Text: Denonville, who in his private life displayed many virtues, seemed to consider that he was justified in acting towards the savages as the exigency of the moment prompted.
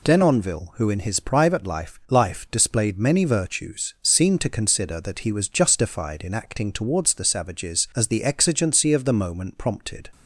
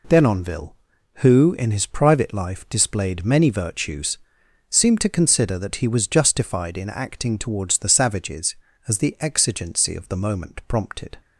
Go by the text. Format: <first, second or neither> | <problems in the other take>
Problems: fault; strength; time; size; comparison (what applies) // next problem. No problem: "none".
second | says "life" twice; at 2.0 s